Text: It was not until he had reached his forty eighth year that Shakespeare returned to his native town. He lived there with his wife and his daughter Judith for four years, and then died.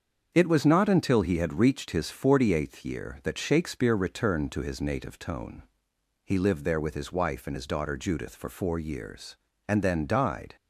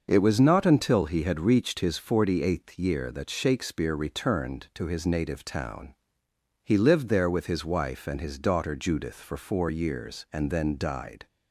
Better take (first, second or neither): second